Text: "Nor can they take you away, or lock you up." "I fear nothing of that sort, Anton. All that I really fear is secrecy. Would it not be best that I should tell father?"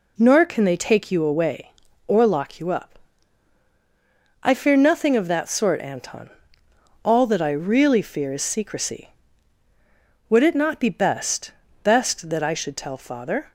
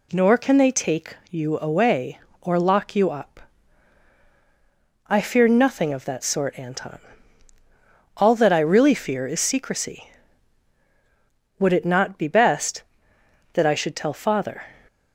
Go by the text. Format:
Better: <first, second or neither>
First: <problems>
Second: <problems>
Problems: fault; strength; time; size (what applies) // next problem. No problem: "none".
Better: second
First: says "best" twice; at 11.8 s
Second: none